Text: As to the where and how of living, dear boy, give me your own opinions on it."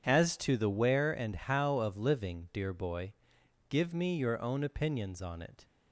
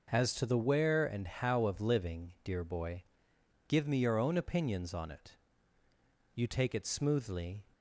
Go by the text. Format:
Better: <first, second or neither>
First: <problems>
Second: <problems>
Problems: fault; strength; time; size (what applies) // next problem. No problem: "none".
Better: first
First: none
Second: goes on to say "You take it smoothly"; from 6.3 s on; 1.3 s long